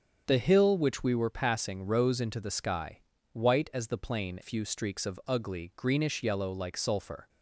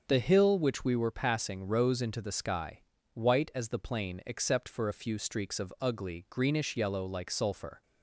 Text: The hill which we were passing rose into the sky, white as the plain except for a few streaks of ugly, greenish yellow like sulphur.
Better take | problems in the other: second | starts louder than the rest; strong; until 1.2 s; 7 dB; also in the second // skips "except for a"; at 4.3 s

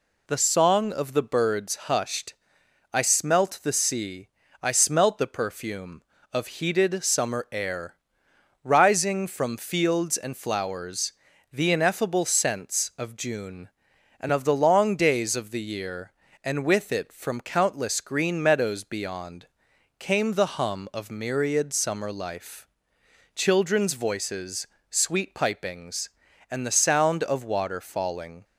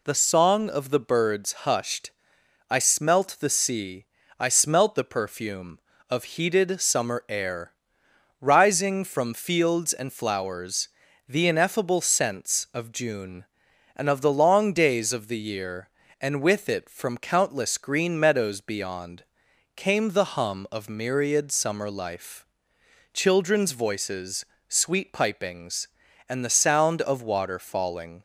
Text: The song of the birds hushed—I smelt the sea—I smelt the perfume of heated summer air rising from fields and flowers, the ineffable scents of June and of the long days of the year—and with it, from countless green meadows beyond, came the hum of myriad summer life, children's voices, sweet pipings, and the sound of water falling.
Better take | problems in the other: neither | pauses between "air" and "rising"; noticeable; the same in both

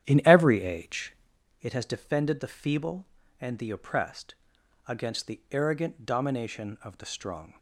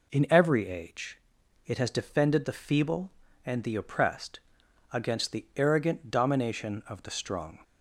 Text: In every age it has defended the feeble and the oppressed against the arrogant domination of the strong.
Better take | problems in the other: second | starts louder than the rest; strong; until 1.4 s; 10.5 dB // pauses between "age" and "it"; noticeable; at 1.1 s; 0.48 s long; noticeable in the second // pauses between "oppressed" and "against"; noticeable; at 4.3 s; 0.52 s long; noticeable in the second

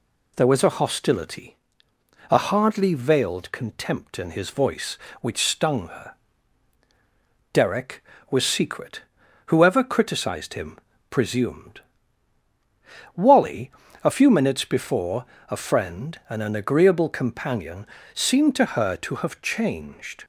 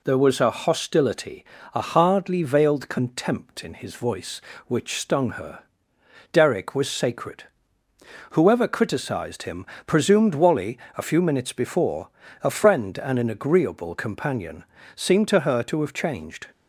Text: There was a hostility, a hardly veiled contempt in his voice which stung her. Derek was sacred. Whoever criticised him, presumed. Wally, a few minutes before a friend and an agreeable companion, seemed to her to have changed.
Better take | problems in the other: second | says "secret" for "sacred"; at 8.4 s // pauses between "before" and "a"; slight; at 15.2 s; 0.26 s long; slight in the second

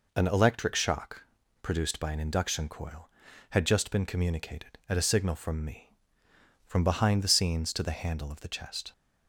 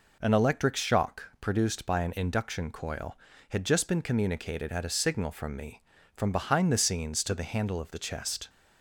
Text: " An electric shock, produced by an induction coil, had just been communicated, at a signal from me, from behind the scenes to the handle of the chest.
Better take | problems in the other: neither | none

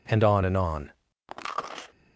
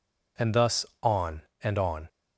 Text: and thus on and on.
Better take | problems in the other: second | skips "thus"; at 0.2 s

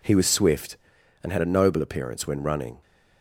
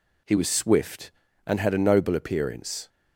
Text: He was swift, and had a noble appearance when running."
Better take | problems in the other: first | stops before "when running"; at 2.8 s

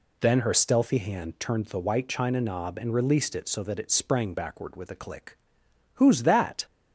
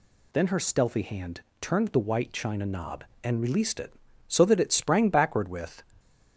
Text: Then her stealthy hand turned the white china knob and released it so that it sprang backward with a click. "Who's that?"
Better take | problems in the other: first | pauses between "hand" and "turned"; slight; at 1.4 s; 0.18 s long // stops before "a click Who's that"; at 5.9 s

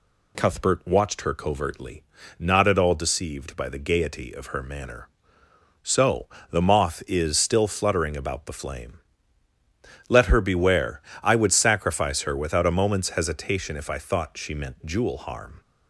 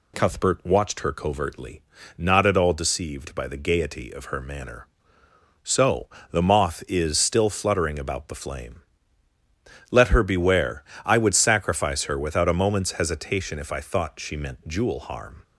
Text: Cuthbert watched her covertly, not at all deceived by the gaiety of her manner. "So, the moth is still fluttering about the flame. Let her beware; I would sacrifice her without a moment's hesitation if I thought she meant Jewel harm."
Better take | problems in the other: neither | none

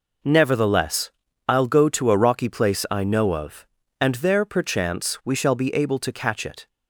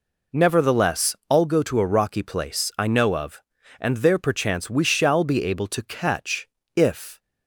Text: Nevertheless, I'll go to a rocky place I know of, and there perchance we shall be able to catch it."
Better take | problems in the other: first | says "if" for "it"; at 6.7 s

